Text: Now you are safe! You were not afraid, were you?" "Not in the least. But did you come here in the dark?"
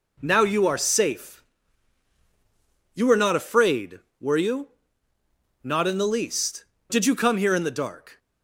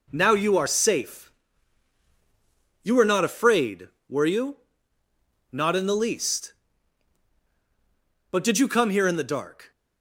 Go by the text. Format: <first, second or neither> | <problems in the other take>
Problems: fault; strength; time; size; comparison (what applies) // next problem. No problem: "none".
second | skips "But"; at 6.7 s